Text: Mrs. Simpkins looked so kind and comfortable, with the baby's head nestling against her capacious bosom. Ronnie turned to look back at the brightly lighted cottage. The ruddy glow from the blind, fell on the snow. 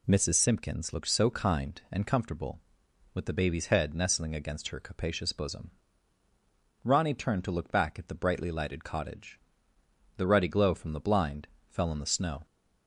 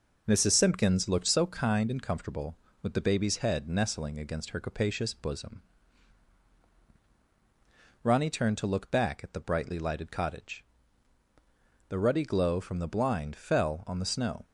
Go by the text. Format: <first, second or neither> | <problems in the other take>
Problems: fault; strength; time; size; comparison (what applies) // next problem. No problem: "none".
neither | none